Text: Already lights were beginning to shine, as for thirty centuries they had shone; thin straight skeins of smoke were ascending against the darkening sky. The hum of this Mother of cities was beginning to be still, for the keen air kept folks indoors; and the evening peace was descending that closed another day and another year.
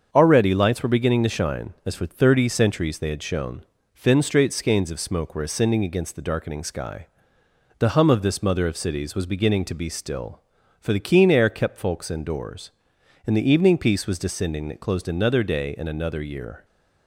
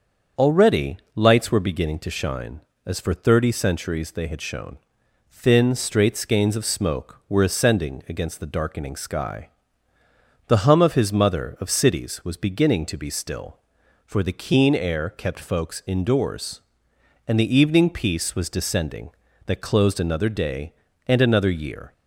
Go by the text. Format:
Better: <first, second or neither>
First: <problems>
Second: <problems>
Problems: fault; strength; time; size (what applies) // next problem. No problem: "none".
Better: first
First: starts louder than the rest; until 1.1 s; 7 dB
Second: starts louder than the rest; until 1.5 s; 7 dB // pauses between "Already" and "lights"; slight; at 0.9 s; 0.18 s long // says "his" for "this"; at 10.9 s